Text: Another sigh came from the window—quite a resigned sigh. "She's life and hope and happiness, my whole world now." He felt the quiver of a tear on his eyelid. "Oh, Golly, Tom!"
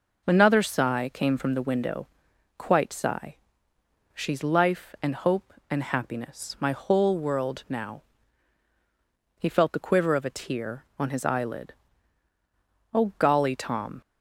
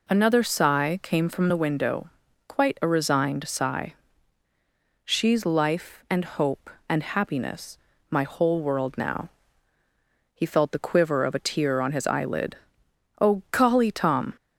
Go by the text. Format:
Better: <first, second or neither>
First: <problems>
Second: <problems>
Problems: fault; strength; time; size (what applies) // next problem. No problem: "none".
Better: second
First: skips "a resigned"; at 2.9 s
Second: none